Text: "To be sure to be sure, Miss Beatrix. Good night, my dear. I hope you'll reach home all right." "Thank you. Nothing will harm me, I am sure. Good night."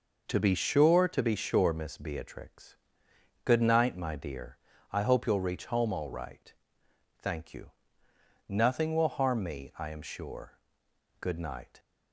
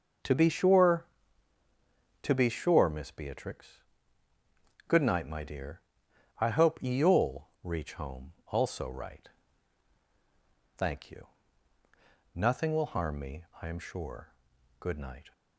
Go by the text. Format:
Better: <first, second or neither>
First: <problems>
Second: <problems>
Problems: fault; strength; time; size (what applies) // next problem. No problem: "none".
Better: first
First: none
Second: says "also" for "all"; at 8.4 s